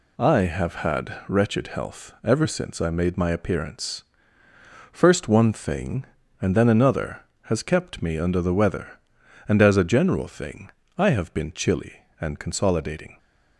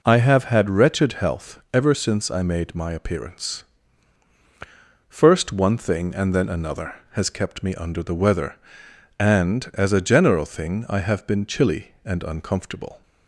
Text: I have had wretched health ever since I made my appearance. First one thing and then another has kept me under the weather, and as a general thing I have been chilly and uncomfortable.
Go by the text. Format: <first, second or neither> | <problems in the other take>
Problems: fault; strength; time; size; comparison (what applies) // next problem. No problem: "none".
second | pauses between "thing" and "I"; slight; at 10.6 s; 0.28 s long // says "consolidating" for "uncomfortable"; at 12.3 s